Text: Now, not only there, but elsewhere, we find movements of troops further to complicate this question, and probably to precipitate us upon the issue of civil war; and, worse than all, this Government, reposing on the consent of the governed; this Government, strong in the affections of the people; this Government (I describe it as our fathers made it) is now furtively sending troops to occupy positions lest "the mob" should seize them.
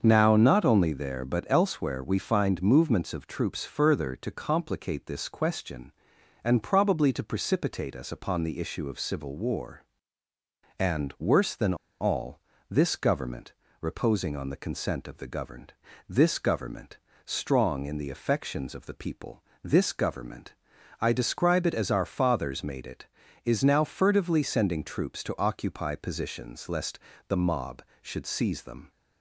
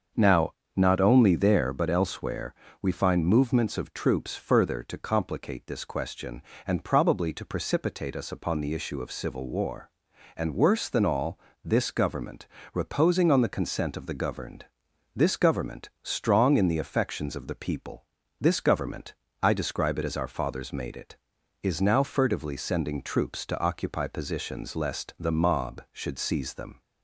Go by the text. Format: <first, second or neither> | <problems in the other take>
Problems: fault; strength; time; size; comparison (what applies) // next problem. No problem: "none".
second | starts louder than the rest; until 1.0 s; 6.5 dB; also in the second // pauses between "than" and "all"; slight; at 11.7 s; 0.26 s long // pauses between "lest" and "the"; slight; at 26.9 s; 0.30 s long